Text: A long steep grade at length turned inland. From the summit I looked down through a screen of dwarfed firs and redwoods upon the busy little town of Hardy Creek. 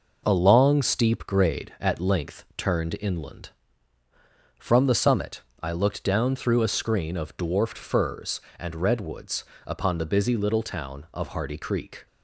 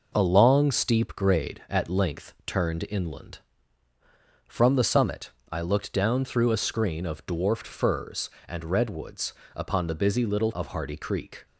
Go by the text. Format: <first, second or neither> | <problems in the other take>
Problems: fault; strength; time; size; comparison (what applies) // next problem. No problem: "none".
first | pauses between "summit" and "I"; slight; at 5.3 s; 0.20 s long; slight in the first // pauses between "redwoods" and "upon"; slight; at 9.3 s; 0.22 s long; slight in the first // skips "town"; at 10.5 s